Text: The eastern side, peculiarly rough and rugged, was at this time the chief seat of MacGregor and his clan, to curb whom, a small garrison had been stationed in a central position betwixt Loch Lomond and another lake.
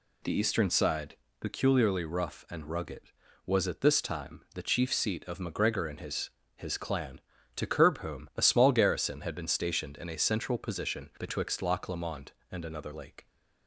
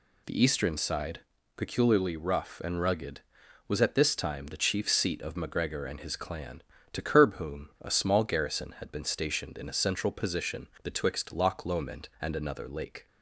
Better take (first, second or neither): second